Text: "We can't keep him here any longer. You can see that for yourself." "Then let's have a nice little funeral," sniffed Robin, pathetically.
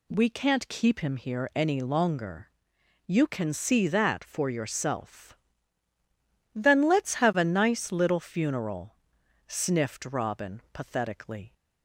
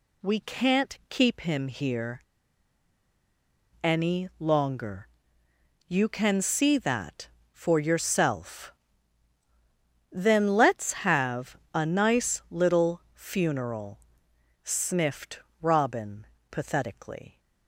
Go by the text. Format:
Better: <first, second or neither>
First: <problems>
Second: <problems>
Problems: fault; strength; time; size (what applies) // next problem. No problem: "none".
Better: first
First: none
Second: pauses between "here" and "any"; strong; at 2.2 s; 1.6 s long // pauses between "have" and "a"; slight; at 11.5 s; 0.16 s long // pauses between "sniffed" and "Robin"; slight; at 15.3 s; 0.22 s long